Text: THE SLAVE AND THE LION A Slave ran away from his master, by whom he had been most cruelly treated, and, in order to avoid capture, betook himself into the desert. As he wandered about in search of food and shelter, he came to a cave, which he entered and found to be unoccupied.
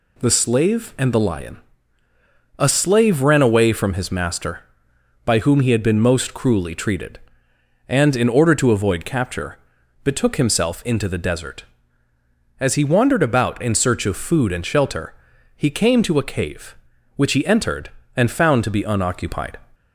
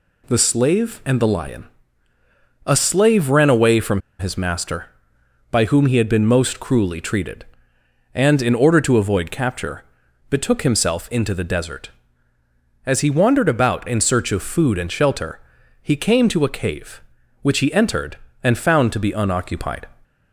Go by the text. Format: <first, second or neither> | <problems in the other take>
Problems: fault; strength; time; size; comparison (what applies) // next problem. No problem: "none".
first | pauses between "LION" and "A"; noticeable; at 1.6 s; 0.98 s long; noticeable in the first // pauses between "from" and "his"; slight; at 4.0 s; 0.18 s long